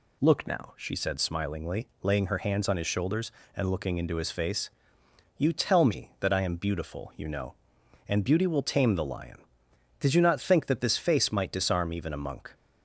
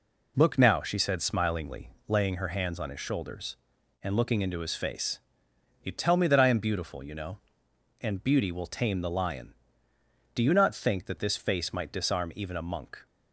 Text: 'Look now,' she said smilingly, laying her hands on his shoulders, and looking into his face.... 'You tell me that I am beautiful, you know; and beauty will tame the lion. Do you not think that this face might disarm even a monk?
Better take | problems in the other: second | says "Did" for "Do"; at 9.9 s

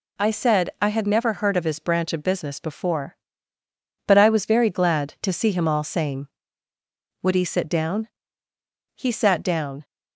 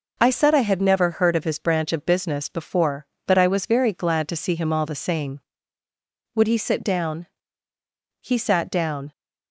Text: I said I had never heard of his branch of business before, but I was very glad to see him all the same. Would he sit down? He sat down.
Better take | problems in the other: second | skips "the"; at 5.8 s

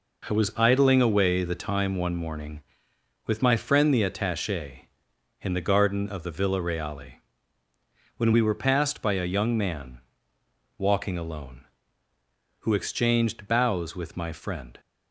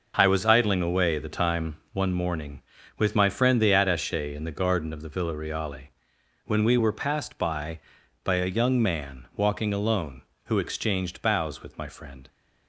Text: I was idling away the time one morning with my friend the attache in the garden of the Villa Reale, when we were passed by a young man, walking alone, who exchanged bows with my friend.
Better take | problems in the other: first | pauses between "time" and "one"; slight; at 1.7 s; 0.16 s long // says "by" twice; at 8.2 s

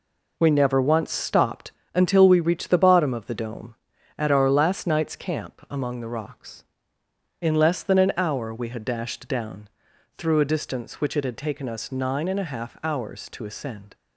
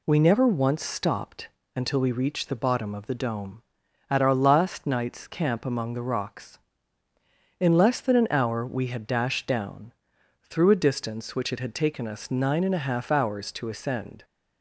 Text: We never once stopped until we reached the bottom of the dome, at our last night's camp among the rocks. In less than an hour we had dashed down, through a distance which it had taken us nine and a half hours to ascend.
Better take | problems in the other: second | gets quieter; strong; throughout; 8 dB // pauses between "stopped" and "until"; slight; at 1.7 s; 0.24 s long; slight in the second

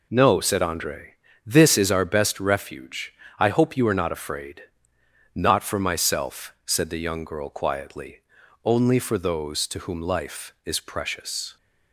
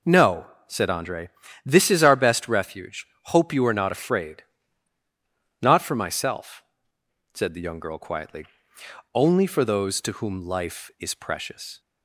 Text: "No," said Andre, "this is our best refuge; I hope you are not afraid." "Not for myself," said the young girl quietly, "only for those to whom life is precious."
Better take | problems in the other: first | skips "I"; at 3.1 s

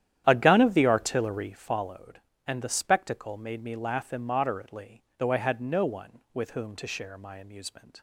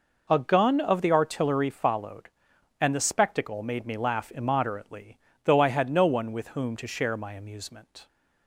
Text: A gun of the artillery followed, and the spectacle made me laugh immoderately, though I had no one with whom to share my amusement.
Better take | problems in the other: second | starts louder than the rest; strong; until 1.6 s; 11 dB

